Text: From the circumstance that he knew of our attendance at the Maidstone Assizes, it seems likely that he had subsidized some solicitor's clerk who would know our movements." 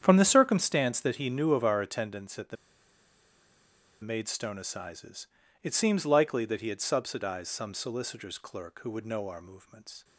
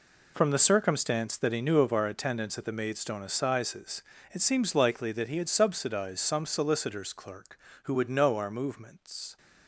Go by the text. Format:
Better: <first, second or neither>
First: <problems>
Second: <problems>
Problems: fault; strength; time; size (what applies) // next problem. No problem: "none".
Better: second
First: starts louder than the rest; strong; until 1.0 s; 9 dB // pauses between "the" and "Maidstone"; strong; at 2.5 s; 1.4 s long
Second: none